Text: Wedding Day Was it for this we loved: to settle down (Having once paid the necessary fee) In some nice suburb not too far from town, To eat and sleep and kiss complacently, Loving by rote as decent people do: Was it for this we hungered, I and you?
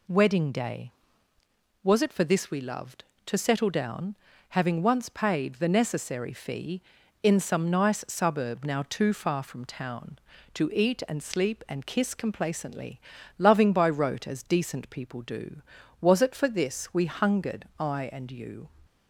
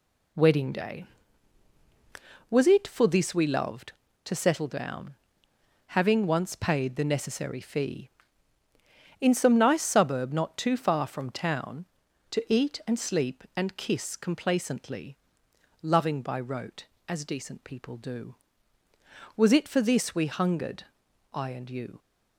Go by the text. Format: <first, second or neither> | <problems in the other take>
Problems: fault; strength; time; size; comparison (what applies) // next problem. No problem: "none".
second | says "now" for "not"; at 8.6 s